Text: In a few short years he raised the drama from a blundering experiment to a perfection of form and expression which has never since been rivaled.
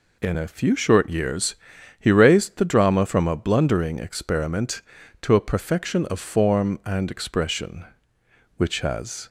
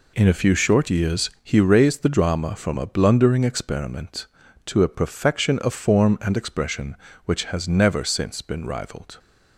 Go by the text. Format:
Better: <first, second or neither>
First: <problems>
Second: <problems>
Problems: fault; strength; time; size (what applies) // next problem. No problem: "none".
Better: second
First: pauses between "years" and "he"; noticeable; at 1.5 s; 0.46 s long // stops before "never since been rivaled"; at 9.2 s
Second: none